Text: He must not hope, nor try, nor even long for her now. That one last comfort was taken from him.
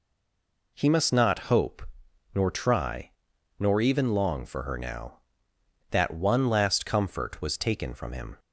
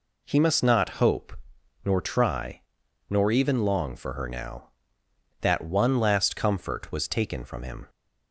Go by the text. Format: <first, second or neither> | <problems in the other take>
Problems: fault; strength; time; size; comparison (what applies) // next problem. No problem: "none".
second | stays silent before the first word; slight; until 0.7 s; 0.7 s long